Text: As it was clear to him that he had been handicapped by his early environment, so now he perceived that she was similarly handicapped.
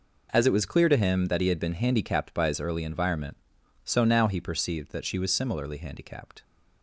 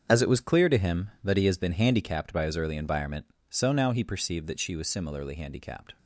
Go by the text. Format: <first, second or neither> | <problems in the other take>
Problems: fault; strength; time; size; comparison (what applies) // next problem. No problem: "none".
first | starts louder than the rest; strong; until 1.0 s; 7.5 dB // says "has" for "had"; at 1.4 s